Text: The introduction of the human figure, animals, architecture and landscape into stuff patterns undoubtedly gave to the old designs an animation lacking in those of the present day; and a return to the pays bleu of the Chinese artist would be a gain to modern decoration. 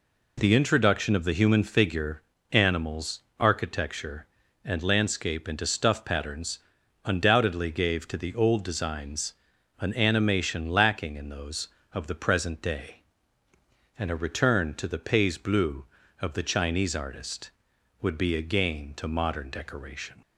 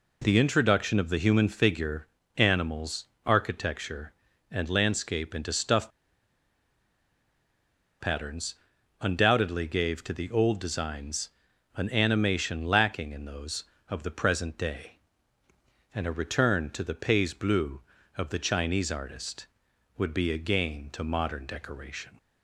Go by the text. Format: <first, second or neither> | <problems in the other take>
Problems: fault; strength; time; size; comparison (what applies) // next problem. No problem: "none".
first | pauses between "stuff" and "patterns"; strong; at 5.9 s; 2.0 s long // pauses between "patterns" and "undoubtedly"; noticeable; at 8.5 s; 0.48 s long; noticeable in the first // pauses between "designs" and "an"; noticeable; at 11.2 s; 0.48 s long; noticeable in the first